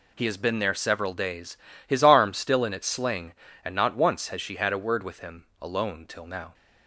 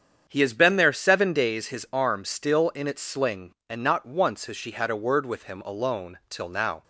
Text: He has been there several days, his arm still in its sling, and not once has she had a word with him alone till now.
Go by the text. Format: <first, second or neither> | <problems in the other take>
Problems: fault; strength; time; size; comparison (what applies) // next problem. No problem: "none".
first | starts louder than the rest; strong; until 1.2 s; 8 dB // says "seven" for "several"; at 0.9 s